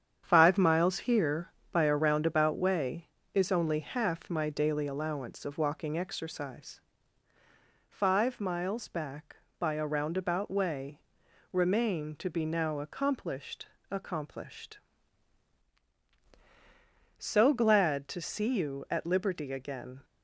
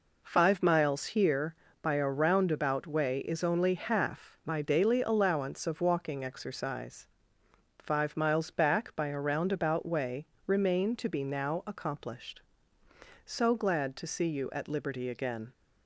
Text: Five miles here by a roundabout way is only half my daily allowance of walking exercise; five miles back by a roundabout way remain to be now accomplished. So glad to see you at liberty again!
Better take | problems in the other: second | starts louder than the rest; strong; until 1.2 s; 8.5 dB // pauses between "way" and "remain"; noticeable; at 11.0 s; 0.52 s long; slight in the second // says "accomplished" twice; at 13.9 s

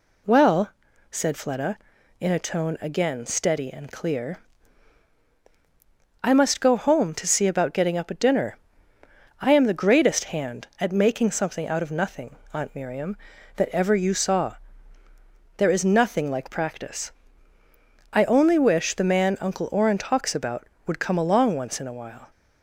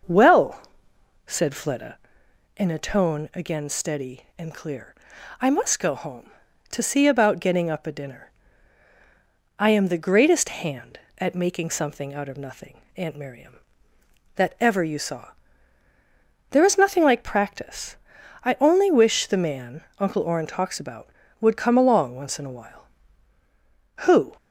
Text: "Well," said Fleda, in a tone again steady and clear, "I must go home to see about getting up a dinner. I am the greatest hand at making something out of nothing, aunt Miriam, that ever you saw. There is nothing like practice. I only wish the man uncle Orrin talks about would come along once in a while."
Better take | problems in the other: first | goes on to say "Who"; slight; from 24.0 s on; 0.36 s long

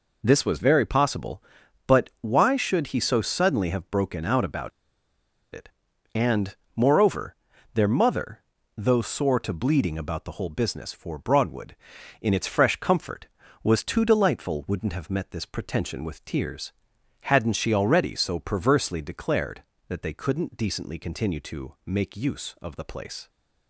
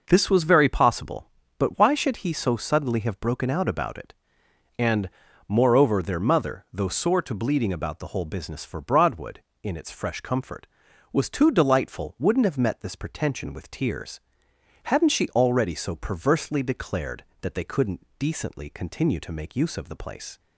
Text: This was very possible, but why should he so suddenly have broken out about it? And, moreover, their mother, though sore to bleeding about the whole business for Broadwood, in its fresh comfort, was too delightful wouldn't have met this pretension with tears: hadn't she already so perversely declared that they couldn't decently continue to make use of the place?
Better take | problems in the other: second | pauses between "about" and "it"; noticeable; at 4.7 s; 0.84 s long

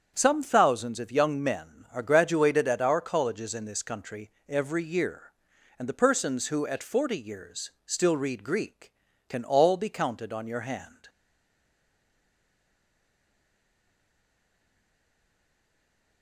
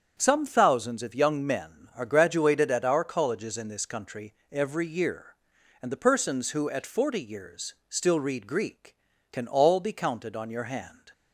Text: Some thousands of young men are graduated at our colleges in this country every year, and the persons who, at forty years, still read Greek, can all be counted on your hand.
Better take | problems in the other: second | starts louder than the rest; strong; until 1.1 s; 7.5 dB; strong in the second // pauses between "country" and "every"; slight; at 4.3 s; 0.16 s long; slight in the second // stays silent after the last word; strong; from 11.0 s on; 5.2 s long

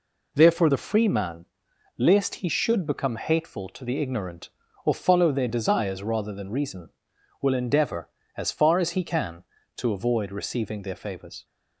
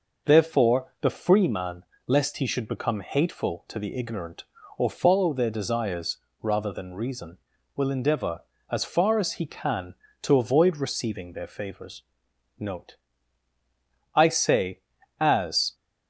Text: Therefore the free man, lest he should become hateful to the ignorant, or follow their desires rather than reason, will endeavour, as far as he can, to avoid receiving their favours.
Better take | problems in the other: first | pauses between "desires" and "rather"; slight; at 6.1 s; 0.24 s long // goes on to say "Note I say as"; strong; from 12.5 s on; 3.1 s long

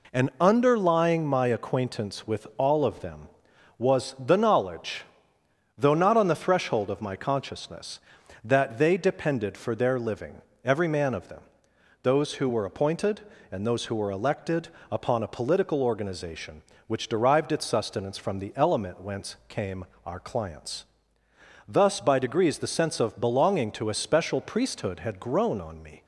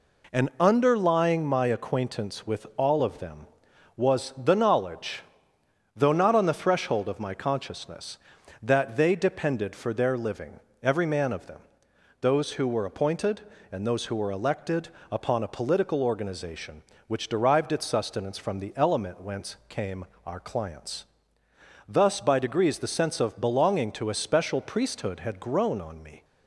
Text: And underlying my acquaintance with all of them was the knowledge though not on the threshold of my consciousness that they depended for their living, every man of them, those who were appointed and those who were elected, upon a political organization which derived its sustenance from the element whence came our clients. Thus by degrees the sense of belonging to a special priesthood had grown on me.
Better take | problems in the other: neither | pauses between "knowledge" and "though"; noticeable; the same in both // pauses between "came" and "our"; slight; the same in both

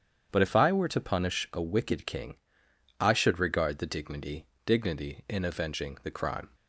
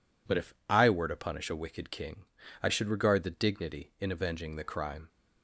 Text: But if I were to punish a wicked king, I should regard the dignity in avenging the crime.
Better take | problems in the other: second | starts louder than the rest; strong; until 1.3 s; 8 dB // says "dignity" twice; at 4.6 s

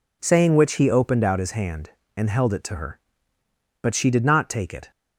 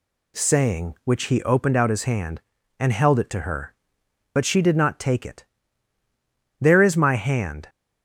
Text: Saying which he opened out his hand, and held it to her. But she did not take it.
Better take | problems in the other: first | goes on to say "There is my hand"; noticeable; from 6.5 s on; 1.1 s long

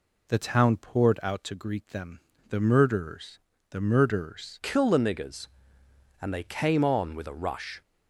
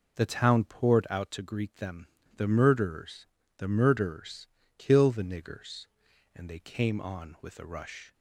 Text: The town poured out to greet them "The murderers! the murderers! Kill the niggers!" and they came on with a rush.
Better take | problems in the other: second | pauses between "them" and "The"; slight; at 2.1 s; 0.30 s long; slight in the second // changes voice at "Kill"; from 4.6 s on; 3.2 s long

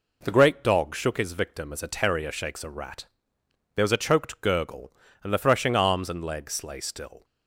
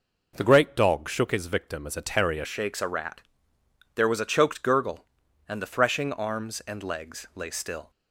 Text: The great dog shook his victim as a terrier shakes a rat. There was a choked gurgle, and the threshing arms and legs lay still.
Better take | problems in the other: first | changes voice at "shakes"; from 2.4 s on; 5.5 s long

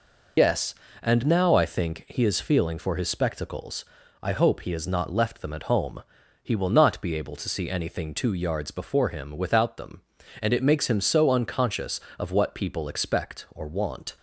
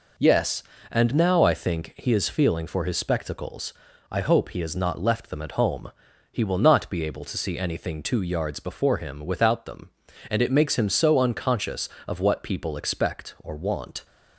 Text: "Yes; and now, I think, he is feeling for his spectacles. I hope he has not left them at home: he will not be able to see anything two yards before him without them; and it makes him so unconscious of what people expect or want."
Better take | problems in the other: second | loses the start of "Yes"; at 0.3 s; 70 ms

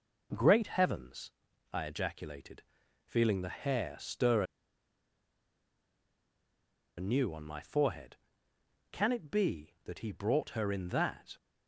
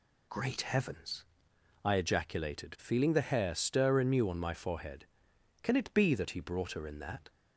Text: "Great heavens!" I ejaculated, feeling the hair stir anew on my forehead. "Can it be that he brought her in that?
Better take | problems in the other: second | pauses between "stir" and "anew"; strong; at 4.4 s; 2.5 s long

